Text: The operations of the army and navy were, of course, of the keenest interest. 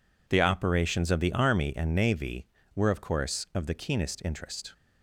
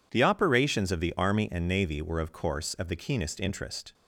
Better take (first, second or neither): neither